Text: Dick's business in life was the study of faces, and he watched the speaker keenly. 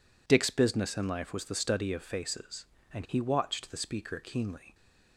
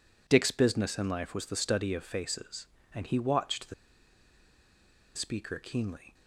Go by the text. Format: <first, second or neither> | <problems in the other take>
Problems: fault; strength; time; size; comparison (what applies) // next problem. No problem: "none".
first | pauses between "the" and "speaker"; strong; at 3.7 s; 1.4 s long